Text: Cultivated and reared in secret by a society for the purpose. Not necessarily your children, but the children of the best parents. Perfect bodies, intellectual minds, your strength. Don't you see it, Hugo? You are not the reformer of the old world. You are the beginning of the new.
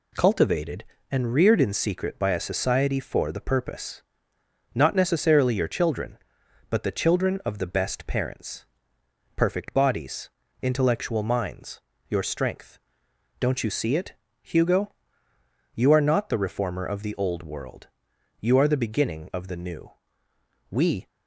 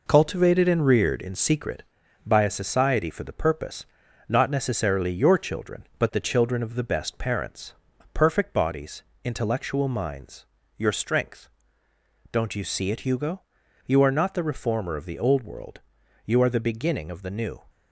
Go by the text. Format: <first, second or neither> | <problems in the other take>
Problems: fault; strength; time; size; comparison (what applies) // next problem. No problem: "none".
second | goes on to say "We"; slight; from 20.6 s on; 0.38 s long